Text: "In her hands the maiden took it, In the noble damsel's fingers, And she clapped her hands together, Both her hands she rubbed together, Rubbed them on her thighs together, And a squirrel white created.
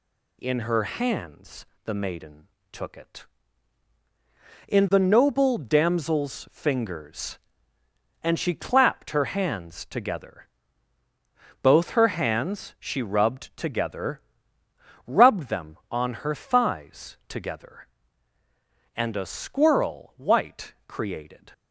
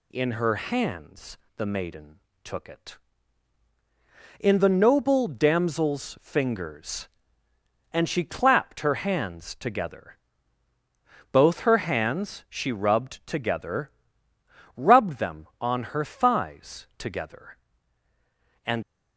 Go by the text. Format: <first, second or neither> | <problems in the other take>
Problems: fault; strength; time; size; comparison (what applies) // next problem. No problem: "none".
first | pauses between "hands" and "the"; slight; at 1.3 s; 0.20 s long; slight in the first // pauses between "maiden" and "took"; slight; at 2.1 s; 0.24 s long; slight in the first // stops before "a squirrel white created"; at 18.8 s